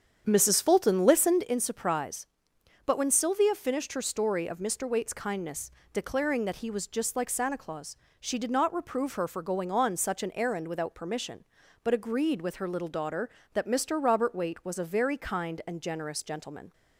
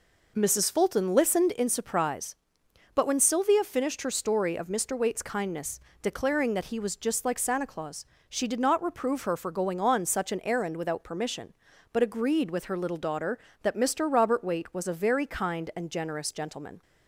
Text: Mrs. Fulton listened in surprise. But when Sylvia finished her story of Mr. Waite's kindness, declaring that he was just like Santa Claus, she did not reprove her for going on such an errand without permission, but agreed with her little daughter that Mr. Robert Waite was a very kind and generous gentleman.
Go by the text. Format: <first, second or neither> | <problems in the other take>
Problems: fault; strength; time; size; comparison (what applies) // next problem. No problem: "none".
second | starts louder than the rest; strong; until 1.4 s; 8 dB